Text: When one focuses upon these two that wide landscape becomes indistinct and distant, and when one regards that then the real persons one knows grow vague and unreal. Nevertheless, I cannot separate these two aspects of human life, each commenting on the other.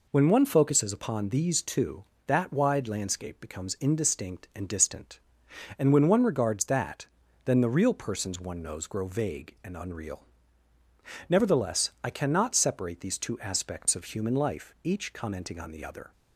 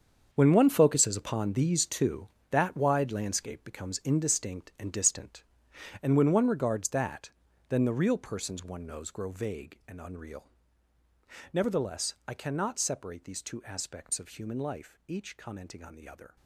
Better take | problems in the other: first | gets quieter; strong; throughout; 12.5 dB // pauses between "that" and "then"; slight; at 7.3 s; 0.36 s long; slight in the first

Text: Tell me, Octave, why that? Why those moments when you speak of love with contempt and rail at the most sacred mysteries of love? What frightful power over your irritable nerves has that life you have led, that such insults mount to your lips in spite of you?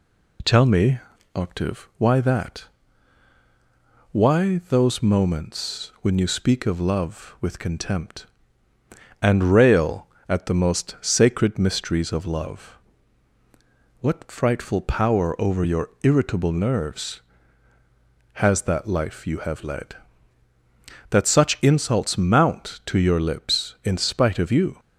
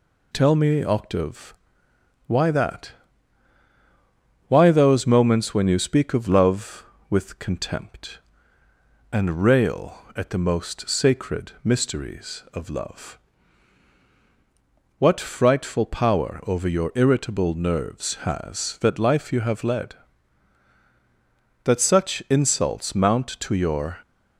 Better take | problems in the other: first | stops before "lips in spite of you"; at 24.0 s

